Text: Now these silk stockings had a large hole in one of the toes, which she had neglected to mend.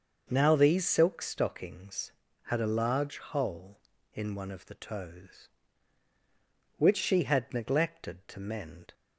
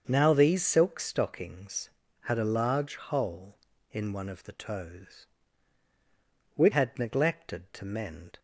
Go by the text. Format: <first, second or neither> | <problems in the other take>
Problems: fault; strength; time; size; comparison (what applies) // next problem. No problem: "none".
first | starts louder than the rest; until 1.0 s; 7 dB; also in the first // skips "she"; at 6.7 s